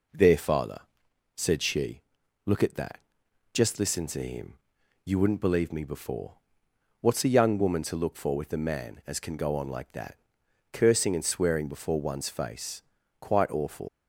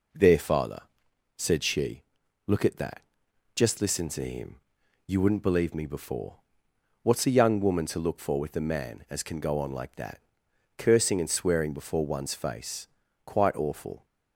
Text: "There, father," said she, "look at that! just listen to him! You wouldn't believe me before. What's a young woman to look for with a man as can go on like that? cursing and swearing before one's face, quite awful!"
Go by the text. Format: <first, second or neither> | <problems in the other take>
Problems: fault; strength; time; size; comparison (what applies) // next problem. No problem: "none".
second | leaves "awful" unfinished; at 13.8 s; 110 ms